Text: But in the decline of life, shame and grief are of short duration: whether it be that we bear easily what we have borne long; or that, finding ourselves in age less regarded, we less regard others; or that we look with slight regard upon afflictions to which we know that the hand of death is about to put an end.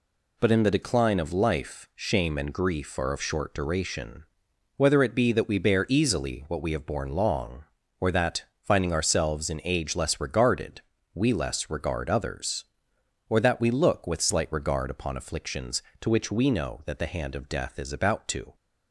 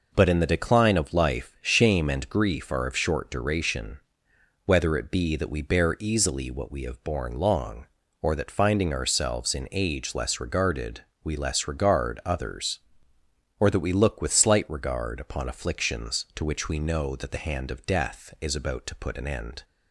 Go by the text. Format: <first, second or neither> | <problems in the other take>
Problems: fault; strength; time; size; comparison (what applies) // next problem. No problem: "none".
second | stops before "put an end"; at 18.5 s